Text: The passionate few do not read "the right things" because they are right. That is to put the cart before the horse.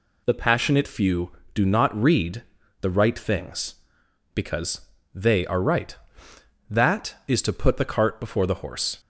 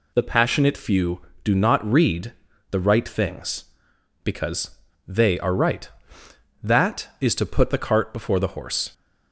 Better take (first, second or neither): neither